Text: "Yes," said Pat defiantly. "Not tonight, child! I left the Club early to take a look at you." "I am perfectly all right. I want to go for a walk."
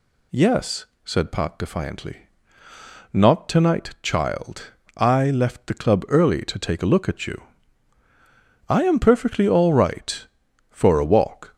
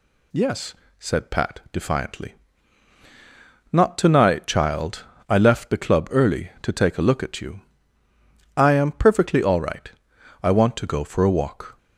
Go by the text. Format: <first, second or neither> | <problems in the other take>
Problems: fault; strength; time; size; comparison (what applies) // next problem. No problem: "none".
second | skips "I want to go"; at 10.4 s